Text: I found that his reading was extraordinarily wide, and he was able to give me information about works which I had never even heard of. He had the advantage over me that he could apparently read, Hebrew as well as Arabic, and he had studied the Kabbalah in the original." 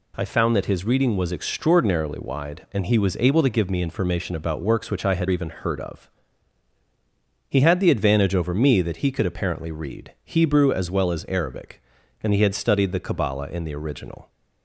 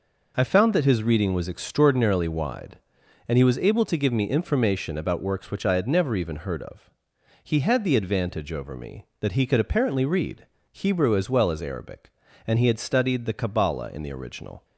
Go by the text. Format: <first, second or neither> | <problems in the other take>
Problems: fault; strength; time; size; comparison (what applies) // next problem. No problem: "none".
second | skips "never"; at 5.2 s